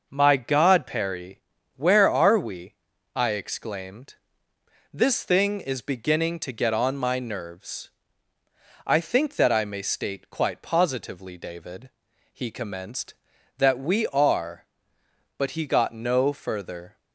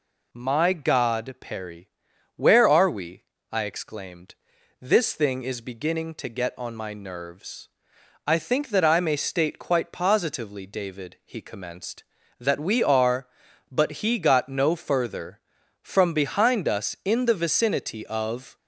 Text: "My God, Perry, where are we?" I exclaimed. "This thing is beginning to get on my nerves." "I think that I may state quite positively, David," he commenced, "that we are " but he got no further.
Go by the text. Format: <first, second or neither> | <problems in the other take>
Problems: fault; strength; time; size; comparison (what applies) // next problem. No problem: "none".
first | goes on to say "From behind us in the vicinity of"; strong; from 15.8 s on; 2.7 s long